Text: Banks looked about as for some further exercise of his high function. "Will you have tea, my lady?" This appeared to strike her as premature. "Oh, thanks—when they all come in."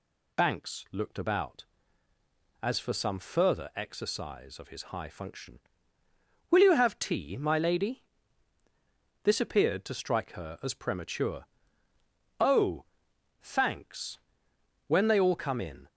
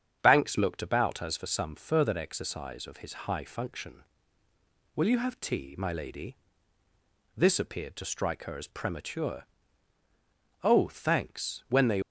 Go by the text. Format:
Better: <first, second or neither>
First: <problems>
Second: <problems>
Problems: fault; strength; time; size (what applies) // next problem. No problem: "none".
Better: first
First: none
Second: starts louder than the rest; strong; until 1.2 s; 7.5 dB // stops before "all come in"; at 12.0 s